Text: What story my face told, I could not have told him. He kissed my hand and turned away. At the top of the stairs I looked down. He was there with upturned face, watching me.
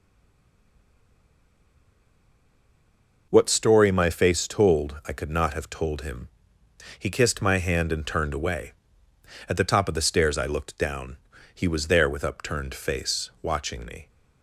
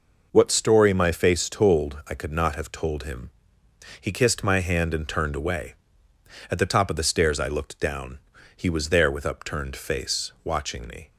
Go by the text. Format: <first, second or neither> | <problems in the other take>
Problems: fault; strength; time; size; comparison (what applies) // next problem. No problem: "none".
second | stays silent before the first word; strong; until 3.3 s; 3.3 s long